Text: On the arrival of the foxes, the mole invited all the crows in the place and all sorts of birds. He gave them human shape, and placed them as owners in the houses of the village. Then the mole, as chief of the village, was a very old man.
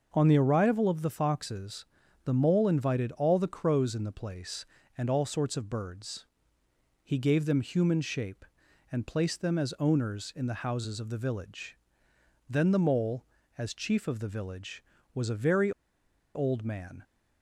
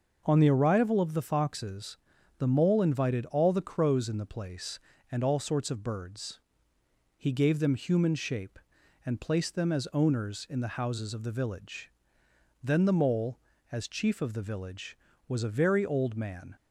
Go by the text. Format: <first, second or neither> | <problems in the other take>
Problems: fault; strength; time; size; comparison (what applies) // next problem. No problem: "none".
second | starts louder than the rest; noticeable; until 1.1 s; 6 dB; noticeable in the second // pauses between "very" and "old"; noticeable; at 15.7 s; 0.63 s long